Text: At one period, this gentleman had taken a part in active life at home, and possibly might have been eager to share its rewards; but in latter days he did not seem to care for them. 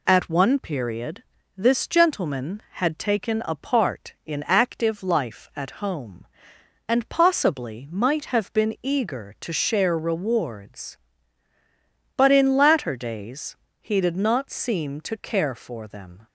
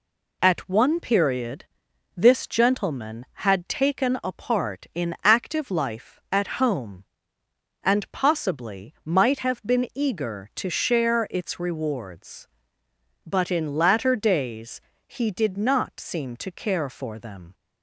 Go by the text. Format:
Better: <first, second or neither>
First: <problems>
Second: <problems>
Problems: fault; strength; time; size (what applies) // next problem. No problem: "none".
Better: second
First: skips "its"; at 9.9 s // pauses between "days" and "he"; slight; at 13.5 s; 0.26 s long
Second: pauses between "days" and "he"; slight; at 14.7 s; 0.28 s long